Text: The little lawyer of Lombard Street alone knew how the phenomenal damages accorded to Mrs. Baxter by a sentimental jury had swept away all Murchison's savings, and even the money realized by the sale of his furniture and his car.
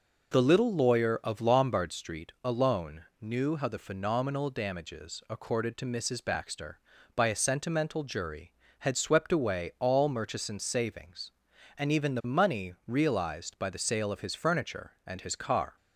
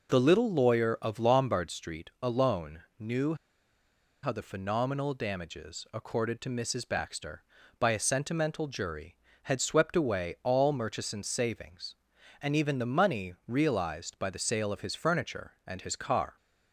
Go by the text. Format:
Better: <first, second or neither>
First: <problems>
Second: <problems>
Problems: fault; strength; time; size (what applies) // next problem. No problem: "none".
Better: first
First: pauses between "alone" and "knew"; slight; at 3.0 s; 0.16 s long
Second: pauses between "alone" and "knew"; slight; at 2.8 s; 0.16 s long // pauses between "knew" and "how"; noticeable; at 3.3 s; 0.88 s long